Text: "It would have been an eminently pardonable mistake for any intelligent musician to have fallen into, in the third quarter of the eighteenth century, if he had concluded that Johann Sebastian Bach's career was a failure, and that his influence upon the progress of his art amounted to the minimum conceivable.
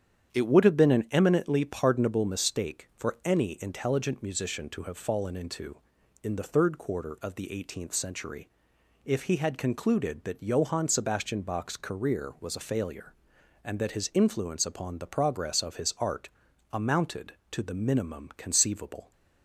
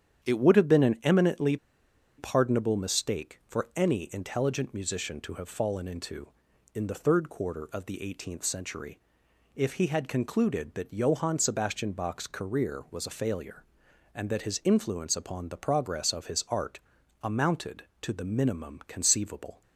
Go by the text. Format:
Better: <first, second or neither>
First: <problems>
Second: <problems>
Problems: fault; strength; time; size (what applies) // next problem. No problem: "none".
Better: first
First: starts louder than the rest; strong; until 1.3 s; 9 dB // pauses between "art" and "amounted"; at 16.2 s; 0.42 s long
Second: starts louder than the rest; strong; until 1.2 s; 9 dB // pauses between "eminently" and "pardonable"; noticeable; at 1.5 s; 0.62 s long // pauses between "art" and "amounted"; at 16.7 s; 0.42 s long